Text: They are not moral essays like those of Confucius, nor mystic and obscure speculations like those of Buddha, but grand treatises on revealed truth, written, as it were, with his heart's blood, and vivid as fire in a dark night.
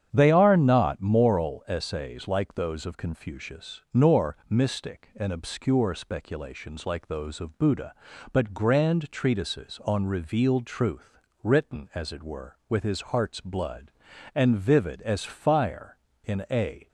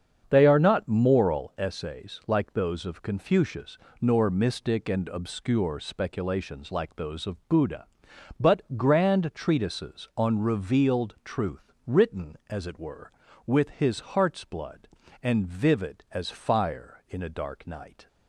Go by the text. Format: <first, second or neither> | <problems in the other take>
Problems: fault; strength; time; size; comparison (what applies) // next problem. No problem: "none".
second | starts louder than the rest; strong; until 1.1 s; 8.5 dB; strong in the second // stops before "dark night"; at 16.8 s